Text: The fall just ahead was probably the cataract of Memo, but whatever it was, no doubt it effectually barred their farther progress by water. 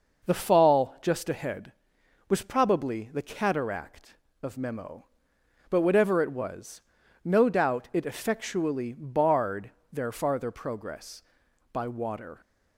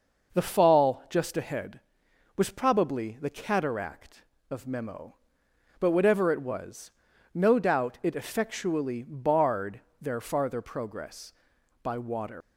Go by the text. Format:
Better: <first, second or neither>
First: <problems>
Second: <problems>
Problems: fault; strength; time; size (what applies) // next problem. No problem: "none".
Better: first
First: pauses between "barred" and "their"; slight; at 9.6 s; 0.22 s long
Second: pauses between "barred" and "their"; slight; at 9.7 s; 0.21 s long // leaves "water" unfinished; at 12.4 s; 105 ms